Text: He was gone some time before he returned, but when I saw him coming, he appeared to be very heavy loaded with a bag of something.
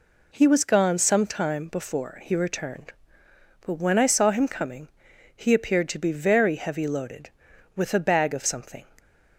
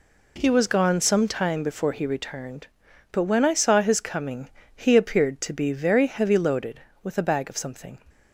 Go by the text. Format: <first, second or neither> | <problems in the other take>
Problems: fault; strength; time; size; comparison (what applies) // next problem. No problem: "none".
first | says "his" for "him"; at 3.8 s